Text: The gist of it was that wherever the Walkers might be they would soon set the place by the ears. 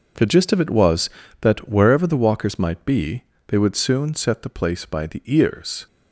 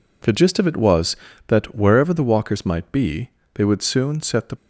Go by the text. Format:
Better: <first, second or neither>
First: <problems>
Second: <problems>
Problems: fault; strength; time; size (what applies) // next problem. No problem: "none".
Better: first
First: pauses between "be" and "they"; slight; at 3.2 s; 0.24 s long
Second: pauses between "be" and "they"; slight; at 3.3 s; 0.24 s long // stops before "place by the ears"; at 4.5 s